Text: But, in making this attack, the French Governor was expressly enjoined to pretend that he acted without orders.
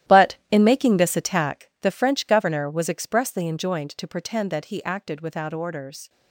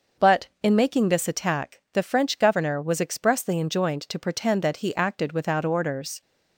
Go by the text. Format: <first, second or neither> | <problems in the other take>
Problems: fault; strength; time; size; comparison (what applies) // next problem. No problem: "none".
second | gets quieter; strong; throughout; 14 dB